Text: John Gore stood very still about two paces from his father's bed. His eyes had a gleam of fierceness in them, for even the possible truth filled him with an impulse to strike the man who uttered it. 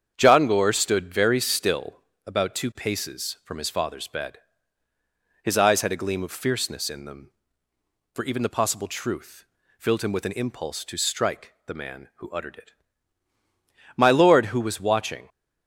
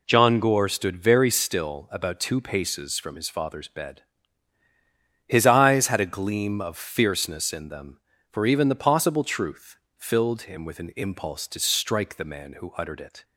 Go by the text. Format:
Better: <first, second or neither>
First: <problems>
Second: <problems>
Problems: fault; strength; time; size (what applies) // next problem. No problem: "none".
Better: second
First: starts louder than the rest; strong; until 1.1 s; 8 dB // pauses between "still" and "about"; slight; at 2.0 s; 0.26 s long // pauses between "truth" and "filled"; slight; at 9.4 s; 0.34 s long // goes on to say "My lord who was watching"; from 13.9 s on; 1.3 s long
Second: pauses between "truth" and "filled"; slight; at 9.7 s; 0.20 s long